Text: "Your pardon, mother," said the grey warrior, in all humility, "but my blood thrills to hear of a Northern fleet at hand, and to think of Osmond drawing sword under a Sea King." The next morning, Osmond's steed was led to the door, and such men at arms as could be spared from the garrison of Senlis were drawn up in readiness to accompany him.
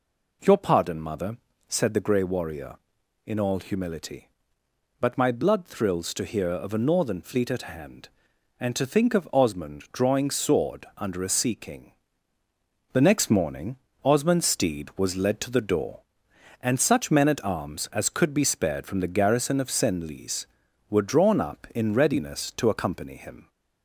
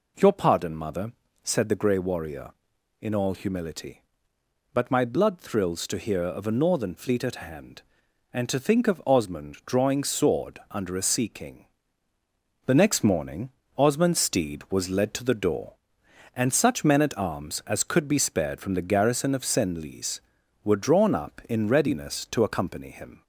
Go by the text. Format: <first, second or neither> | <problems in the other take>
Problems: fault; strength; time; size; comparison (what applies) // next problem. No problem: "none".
neither | none